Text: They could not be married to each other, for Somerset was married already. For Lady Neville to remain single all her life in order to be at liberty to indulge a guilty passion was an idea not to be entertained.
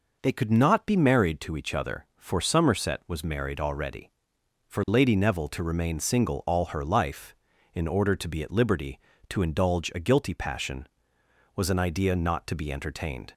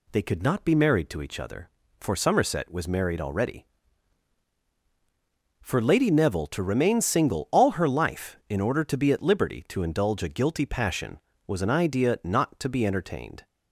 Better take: neither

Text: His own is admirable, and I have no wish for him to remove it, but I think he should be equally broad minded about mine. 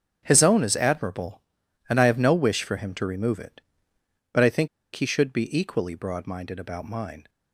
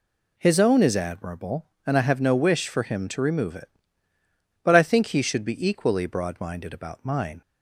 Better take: second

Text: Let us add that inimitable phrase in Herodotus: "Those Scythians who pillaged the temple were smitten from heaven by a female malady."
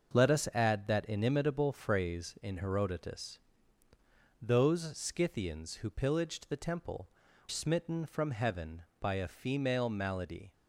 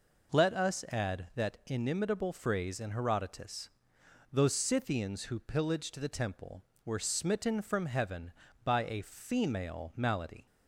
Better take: second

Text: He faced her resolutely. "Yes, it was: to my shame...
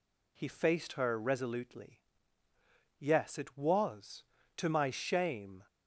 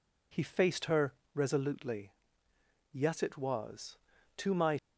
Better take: first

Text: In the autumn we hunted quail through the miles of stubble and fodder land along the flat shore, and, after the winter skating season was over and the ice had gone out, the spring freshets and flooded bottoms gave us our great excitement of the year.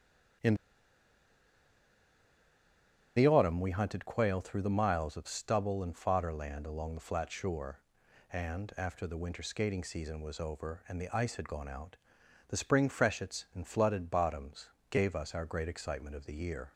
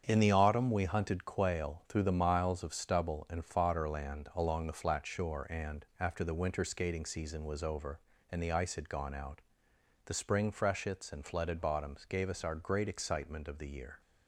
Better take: second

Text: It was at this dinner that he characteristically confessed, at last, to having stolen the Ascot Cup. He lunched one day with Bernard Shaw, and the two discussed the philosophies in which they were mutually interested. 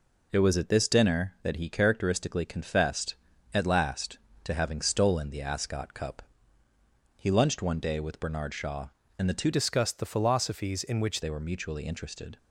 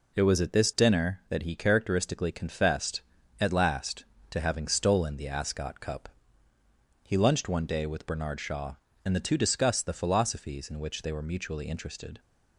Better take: second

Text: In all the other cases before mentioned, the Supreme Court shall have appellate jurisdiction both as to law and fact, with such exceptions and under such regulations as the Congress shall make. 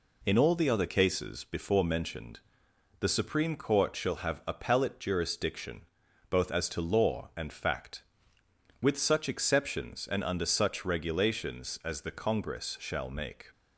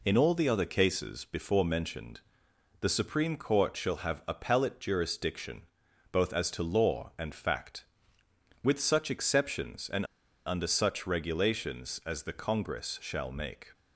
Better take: first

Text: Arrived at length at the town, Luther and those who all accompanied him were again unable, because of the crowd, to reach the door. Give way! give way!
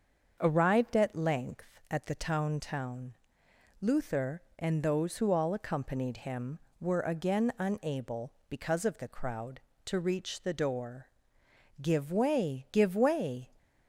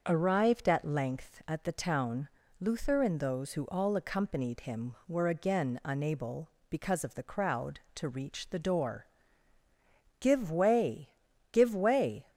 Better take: second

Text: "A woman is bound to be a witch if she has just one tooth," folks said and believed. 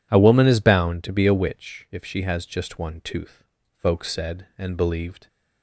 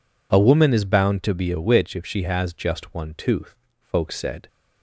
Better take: first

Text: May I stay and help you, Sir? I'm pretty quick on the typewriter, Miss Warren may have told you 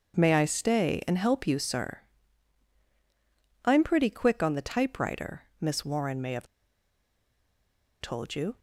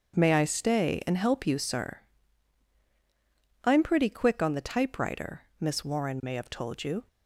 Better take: second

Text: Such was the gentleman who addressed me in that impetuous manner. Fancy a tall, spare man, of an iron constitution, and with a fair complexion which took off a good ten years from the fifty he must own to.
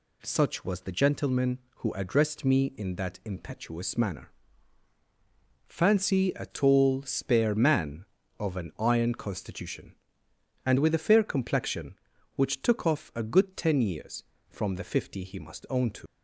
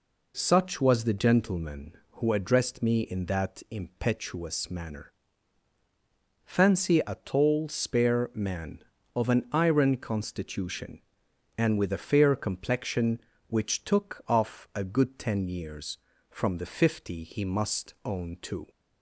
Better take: second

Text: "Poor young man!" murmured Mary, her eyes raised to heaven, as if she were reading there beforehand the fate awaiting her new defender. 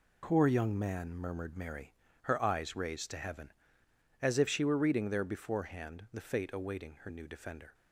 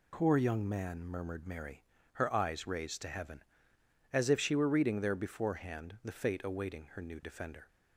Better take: second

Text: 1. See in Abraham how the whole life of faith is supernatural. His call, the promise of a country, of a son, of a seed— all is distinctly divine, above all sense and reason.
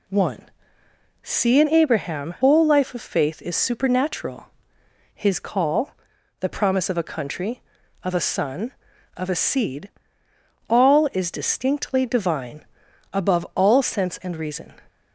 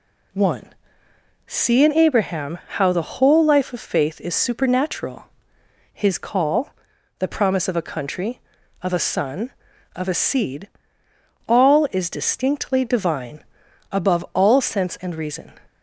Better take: second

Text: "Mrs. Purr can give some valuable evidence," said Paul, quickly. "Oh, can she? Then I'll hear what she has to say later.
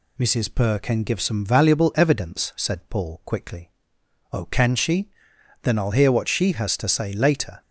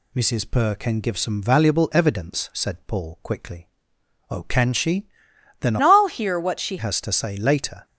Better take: first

